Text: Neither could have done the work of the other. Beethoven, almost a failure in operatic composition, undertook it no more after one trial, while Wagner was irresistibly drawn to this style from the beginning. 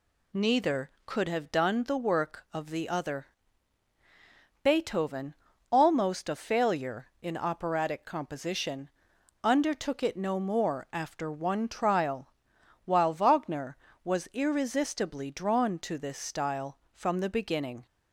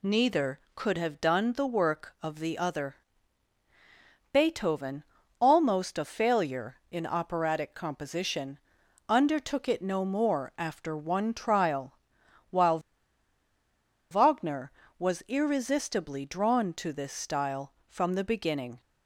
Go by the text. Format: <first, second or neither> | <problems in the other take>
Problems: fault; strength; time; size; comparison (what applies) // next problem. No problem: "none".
first | pauses between "while" and "Wagner"; strong; at 12.7 s; 1.3 s long